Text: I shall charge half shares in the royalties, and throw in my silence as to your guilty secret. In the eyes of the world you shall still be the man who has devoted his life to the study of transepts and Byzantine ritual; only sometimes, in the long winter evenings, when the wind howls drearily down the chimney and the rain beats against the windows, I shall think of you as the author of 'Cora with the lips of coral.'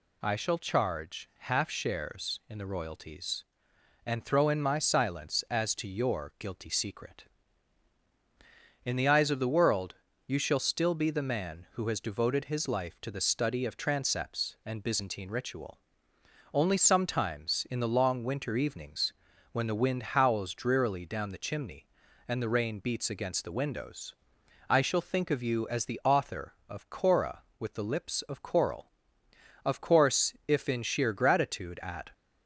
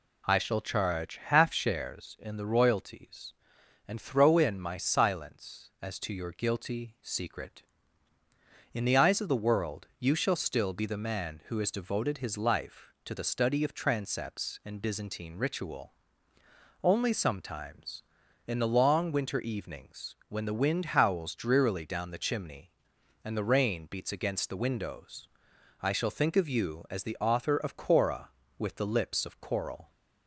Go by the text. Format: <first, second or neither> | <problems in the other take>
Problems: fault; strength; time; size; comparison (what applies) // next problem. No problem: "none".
second | pauses between "world" and "you"; slight; at 9.9 s; 0.32 s long // goes on to say "Of course if in sheer gratitude at"; strong; from 29.6 s on; 2.4 s long